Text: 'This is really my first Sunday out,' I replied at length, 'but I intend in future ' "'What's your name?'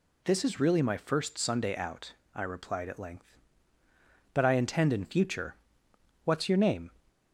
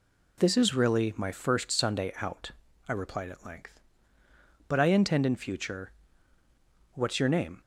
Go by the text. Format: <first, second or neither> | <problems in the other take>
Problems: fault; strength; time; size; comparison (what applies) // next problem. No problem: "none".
neither | none